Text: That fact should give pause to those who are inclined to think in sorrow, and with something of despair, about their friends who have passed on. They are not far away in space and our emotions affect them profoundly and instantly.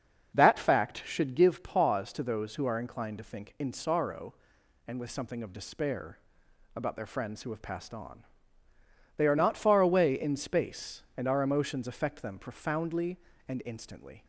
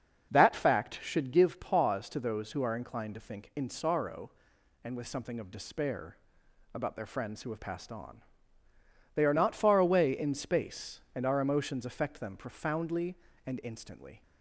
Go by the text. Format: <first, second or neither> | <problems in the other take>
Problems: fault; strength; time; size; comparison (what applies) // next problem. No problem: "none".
neither | starts louder than the rest; the same in both